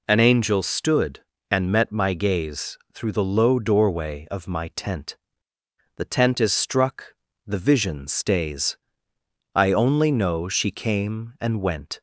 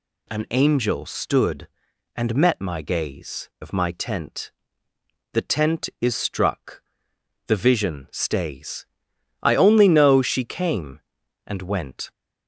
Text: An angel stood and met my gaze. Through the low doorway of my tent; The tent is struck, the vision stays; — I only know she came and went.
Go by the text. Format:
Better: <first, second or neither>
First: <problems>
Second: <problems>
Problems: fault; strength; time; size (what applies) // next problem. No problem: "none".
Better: first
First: none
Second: skips "Through the low doorway"; at 3.5 s